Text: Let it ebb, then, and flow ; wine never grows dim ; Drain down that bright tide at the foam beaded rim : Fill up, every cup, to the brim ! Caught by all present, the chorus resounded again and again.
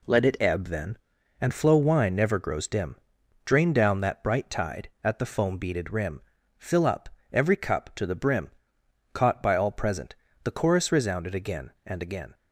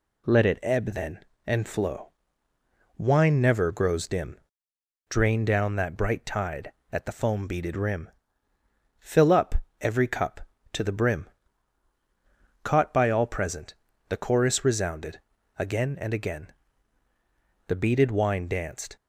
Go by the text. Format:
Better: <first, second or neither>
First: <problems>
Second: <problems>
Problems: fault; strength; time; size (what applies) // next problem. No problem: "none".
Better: first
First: none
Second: pauses between "resounded" and "again"; at 15.1 s; 0.38 s long // goes on to say "The beaded wine danced"; noticeable; from 17.6 s on; 1.2 s long